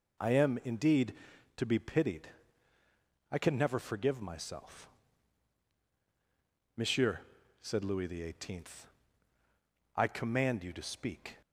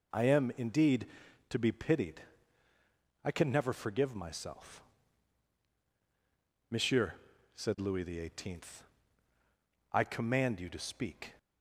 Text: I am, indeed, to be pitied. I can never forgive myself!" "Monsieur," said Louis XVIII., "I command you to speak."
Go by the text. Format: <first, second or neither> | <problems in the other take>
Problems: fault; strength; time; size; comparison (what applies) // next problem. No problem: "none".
neither | none